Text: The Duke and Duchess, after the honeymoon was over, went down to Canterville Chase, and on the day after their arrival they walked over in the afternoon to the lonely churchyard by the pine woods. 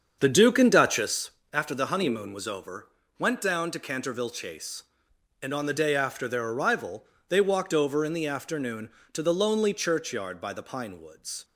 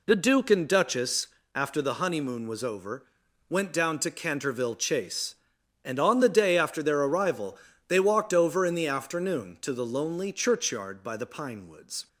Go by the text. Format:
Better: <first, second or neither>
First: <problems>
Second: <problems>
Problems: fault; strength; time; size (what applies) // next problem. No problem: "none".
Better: second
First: starts louder than the rest; strong; until 1.3 s; 7 dB // pauses between "arrival" and "they"; slight; at 7.0 s; 0.24 s long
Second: pauses between "arrival" and "they"; slight; at 7.5 s; 0.32 s long